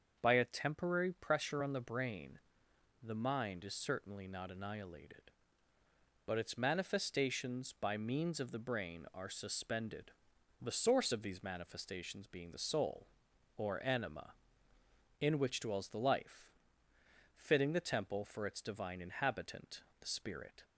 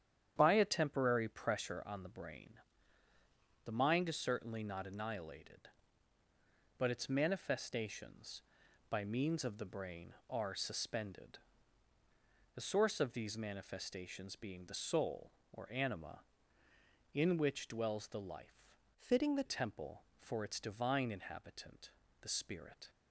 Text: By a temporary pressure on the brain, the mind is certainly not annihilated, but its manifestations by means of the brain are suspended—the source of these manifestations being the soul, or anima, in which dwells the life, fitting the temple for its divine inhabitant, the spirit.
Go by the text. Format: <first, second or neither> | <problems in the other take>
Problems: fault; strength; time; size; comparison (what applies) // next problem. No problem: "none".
first | starts louder than the rest; strong; until 1.3 s; 9.5 dB; also in the first // changes voice from "fitting" to "the"; from 18.9 to 19.4 s; 0.5 s long